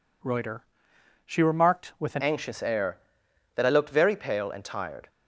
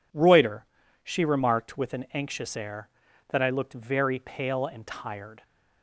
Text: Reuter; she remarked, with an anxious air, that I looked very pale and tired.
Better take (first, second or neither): second